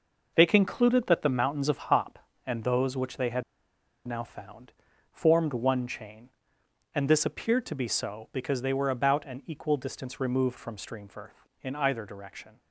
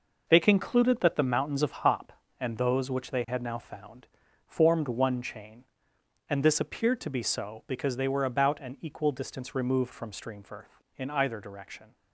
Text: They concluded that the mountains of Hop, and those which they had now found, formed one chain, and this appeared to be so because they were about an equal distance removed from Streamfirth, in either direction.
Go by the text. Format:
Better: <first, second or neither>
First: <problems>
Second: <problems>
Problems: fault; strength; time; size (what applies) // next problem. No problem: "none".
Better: second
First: pauses between "had" and "now"; noticeable; at 3.4 s; 0.64 s long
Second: none